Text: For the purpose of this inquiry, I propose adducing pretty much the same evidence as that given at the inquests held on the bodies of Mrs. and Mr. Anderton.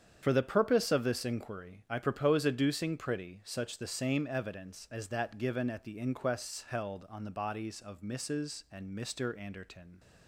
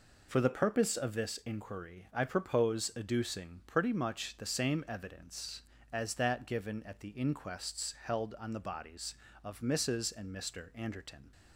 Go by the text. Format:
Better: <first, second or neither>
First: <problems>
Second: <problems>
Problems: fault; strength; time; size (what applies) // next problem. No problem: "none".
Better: second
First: starts louder than the rest; strong; until 1.2 s; 8 dB // says "such" for "much"; at 3.4 s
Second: none